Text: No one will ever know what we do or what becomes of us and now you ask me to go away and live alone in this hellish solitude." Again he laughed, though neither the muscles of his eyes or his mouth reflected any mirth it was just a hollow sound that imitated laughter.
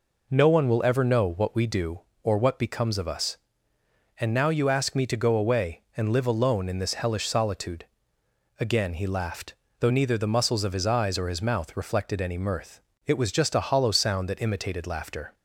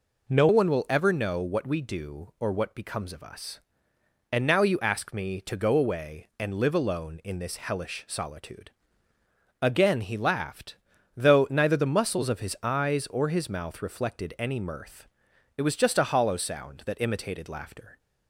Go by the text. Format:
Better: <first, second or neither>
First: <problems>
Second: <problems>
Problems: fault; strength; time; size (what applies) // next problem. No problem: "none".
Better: first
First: pauses between "mirth" and "it"; slight; at 12.7 s; 0.26 s long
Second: changes voice at "one"; from 0.4 s on; 17.5 s long // pauses between "mirth" and "it"; noticeable; at 15.0 s; 0.52 s long